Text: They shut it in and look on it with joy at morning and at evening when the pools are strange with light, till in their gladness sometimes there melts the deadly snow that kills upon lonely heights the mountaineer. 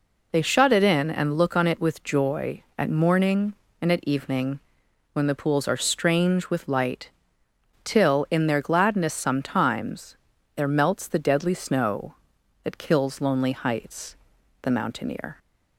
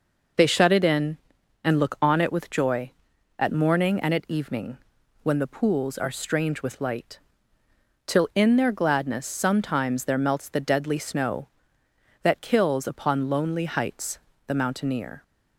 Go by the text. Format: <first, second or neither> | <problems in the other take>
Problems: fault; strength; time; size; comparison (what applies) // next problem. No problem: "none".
second | pauses between "evening" and "when"; noticeable; at 4.6 s; 0.52 s long; noticeable in the second // pauses between "sometimes" and "there"; at 10.1 s; 0.40 s long // skips "upon"; at 13.2 s // pauses between "heights" and "the"; noticeable; at 14.1 s; 0.46 s long; slight in the second